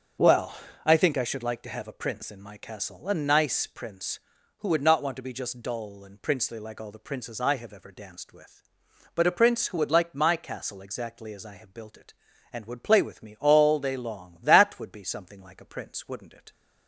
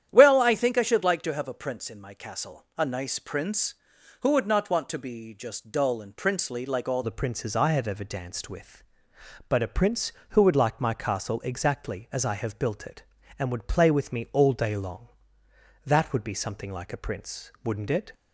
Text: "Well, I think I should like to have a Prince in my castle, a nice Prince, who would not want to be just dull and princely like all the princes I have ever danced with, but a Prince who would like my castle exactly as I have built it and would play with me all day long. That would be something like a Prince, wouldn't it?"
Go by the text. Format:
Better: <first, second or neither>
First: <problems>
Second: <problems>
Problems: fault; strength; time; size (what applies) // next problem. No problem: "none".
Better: first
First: starts louder than the rest; until 1.5 s; 7 dB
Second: starts louder than the rest; strong; until 1.1 s; 10 dB // changes voice at "the"; from 7.0 s on; 11.1 s long